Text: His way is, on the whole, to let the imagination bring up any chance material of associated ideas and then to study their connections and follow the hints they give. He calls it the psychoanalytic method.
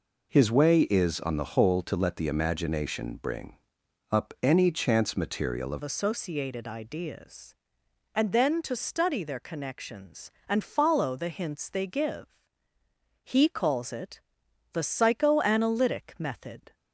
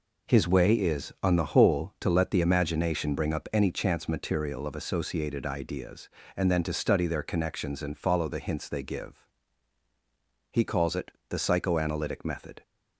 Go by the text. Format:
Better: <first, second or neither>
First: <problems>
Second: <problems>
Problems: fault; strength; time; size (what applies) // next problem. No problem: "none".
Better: second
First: pauses between "bring" and "up"; noticeable; at 3.5 s; 0.56 s long // changes voice at "associated"; from 5.8 s on; 10.9 s long // pauses between "it" and "the"; noticeable; at 14.1 s; 0.54 s long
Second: pauses between "it" and "the"; slight; at 11.1 s; 0.16 s long